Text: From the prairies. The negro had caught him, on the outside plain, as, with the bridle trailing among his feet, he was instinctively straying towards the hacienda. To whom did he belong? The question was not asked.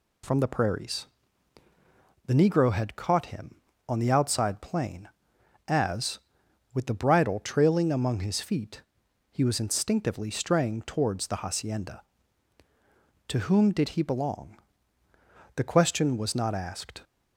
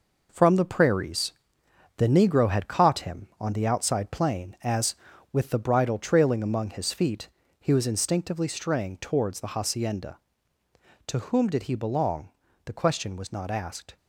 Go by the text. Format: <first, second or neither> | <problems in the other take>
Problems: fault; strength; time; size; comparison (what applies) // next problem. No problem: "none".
first | gets quieter; strong; throughout; 8 dB